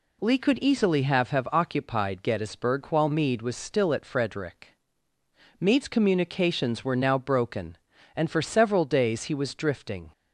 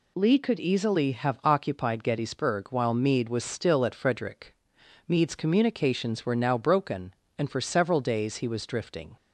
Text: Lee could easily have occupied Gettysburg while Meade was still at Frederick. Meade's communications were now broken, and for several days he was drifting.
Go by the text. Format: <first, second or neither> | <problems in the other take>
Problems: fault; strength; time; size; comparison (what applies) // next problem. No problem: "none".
second | says "have" twice; at 1.3 s